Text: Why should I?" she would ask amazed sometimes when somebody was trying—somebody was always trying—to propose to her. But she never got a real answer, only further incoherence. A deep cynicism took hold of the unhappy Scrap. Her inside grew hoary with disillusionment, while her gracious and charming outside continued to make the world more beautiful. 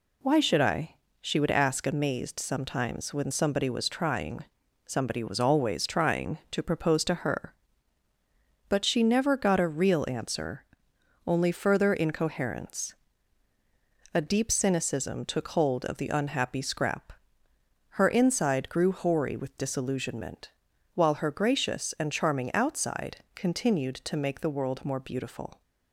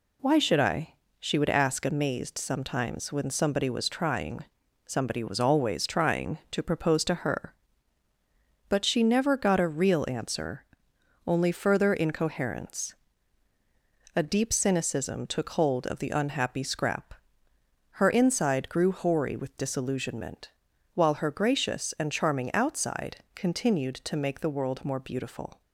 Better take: neither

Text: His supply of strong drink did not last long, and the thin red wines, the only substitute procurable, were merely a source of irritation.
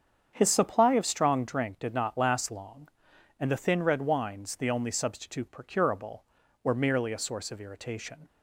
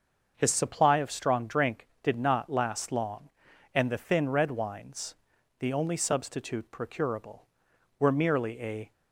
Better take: first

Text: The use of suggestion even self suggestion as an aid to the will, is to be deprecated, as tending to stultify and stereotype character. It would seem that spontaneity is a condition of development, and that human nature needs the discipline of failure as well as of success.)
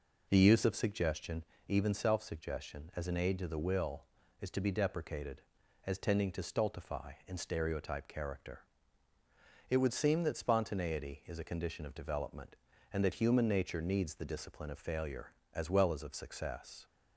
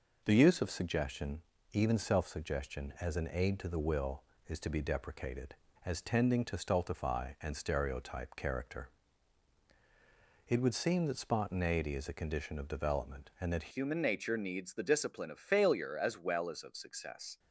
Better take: first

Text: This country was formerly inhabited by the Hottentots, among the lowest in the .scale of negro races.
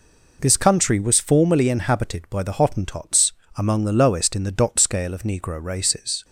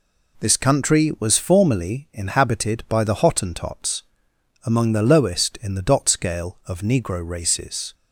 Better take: neither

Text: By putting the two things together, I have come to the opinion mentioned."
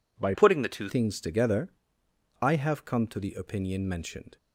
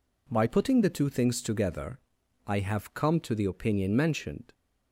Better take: second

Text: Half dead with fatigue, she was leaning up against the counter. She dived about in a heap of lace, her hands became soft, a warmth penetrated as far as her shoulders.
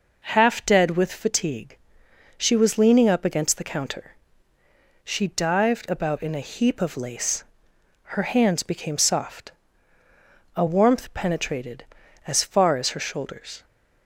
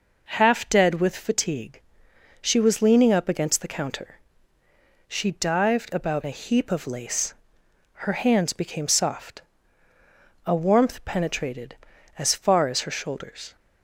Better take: first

